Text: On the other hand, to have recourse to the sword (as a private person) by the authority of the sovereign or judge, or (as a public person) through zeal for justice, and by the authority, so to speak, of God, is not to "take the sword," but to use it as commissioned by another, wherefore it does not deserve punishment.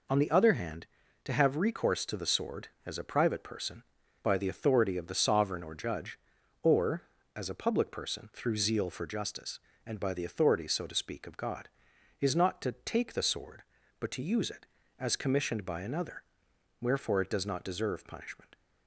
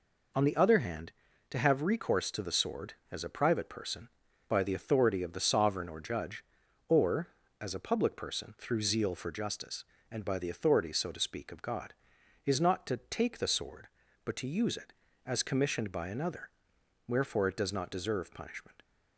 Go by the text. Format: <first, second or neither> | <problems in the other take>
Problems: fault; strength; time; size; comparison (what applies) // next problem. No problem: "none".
neither | none